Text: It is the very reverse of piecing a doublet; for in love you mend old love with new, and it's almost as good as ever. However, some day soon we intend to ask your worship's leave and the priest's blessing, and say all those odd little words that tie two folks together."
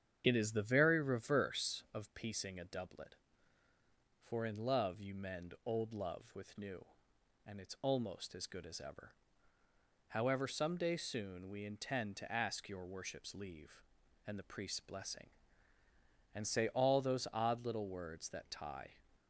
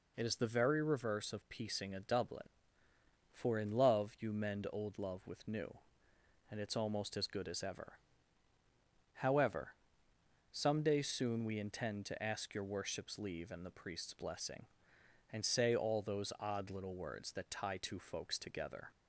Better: second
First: starts louder than the rest; strong; until 1.2 s; 8 dB // stops before "two folks together"; at 19.1 s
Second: none

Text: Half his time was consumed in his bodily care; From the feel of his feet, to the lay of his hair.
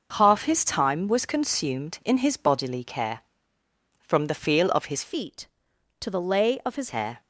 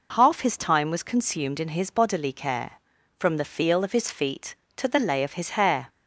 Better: second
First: changes voice from "feet" to "his"; from 5.0 to 6.9 s; 1.9 s long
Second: none

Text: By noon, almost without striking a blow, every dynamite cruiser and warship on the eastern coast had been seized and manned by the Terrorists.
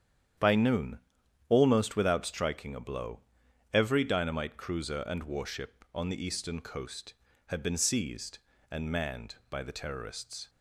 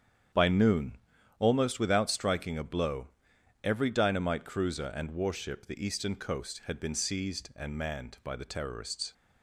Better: first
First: starts louder than the rest; strong; until 1.8 s; 9.5 dB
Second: starts louder than the rest; strong; until 1.7 s; 8.5 dB // skips "on"; at 5.6 s

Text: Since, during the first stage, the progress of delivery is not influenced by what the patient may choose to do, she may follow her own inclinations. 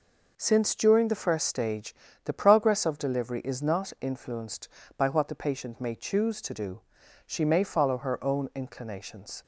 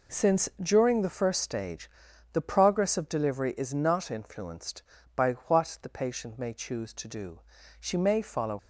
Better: first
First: none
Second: stops before "her own inclinations"; at 8.5 s

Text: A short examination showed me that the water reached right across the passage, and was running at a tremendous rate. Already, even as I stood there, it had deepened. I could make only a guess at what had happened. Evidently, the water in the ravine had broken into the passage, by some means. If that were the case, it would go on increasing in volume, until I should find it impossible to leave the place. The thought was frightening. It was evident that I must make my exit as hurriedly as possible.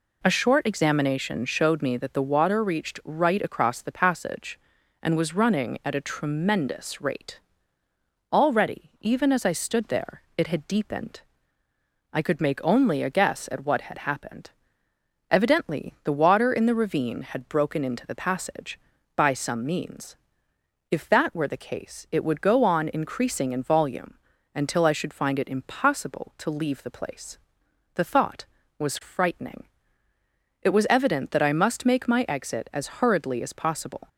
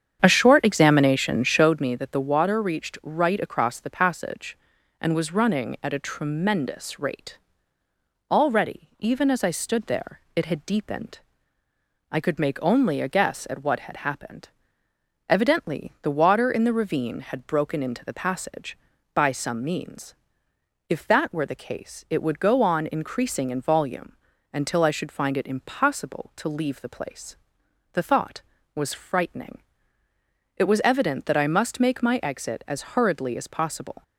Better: first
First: none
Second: starts louder than the rest; strong; until 1.8 s; 8.5 dB

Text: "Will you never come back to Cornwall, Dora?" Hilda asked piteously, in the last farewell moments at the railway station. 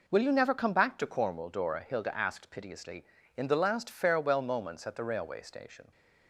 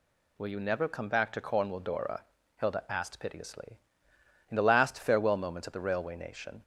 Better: first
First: none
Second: says "nation" for "station"; at 6.1 s

